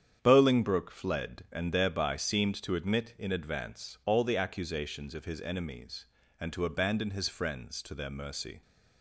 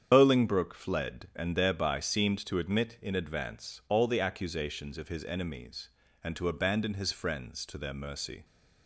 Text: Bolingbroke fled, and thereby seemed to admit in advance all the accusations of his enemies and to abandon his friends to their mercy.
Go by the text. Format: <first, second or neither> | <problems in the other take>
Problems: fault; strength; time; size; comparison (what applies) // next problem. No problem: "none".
first | loses the start of "Bolingbroke"; at 0.1 s; 70 ms // starts louder than the rest; strong; until 1.1 s; 8 dB; strong in the first